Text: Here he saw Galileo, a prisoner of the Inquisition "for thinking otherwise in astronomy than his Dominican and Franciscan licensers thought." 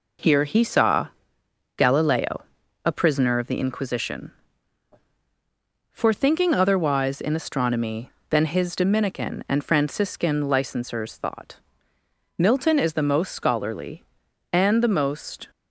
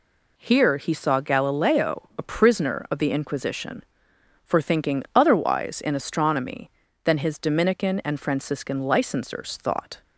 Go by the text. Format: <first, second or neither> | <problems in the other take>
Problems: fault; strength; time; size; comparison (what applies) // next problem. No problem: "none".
second | pauses between "saw" and "Galileo"; noticeable; at 1.0 s; 0.70 s long // goes on to say "Milton is the most scholarly and the most"; strong; from 12.3 s on; 3.1 s long